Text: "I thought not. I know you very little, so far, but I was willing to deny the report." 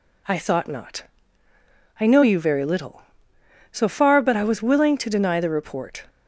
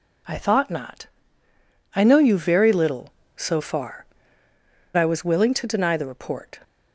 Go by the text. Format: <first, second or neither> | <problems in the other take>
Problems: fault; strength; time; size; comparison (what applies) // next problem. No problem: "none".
first | skips "but"; at 4.5 s